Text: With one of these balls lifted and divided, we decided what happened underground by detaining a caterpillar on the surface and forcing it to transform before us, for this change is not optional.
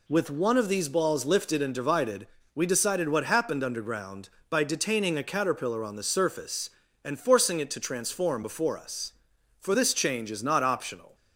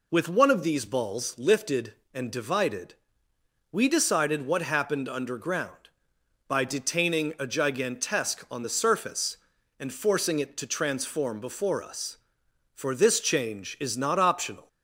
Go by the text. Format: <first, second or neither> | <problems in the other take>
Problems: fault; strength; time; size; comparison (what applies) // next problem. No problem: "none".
first | says "gigantesque" for "caterpillar"; at 7.4 s